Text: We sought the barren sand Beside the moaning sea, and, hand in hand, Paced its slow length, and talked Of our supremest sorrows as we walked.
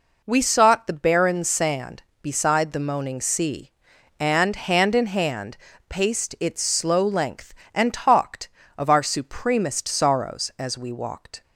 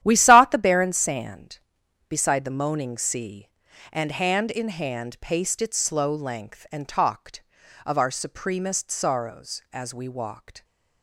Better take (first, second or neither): first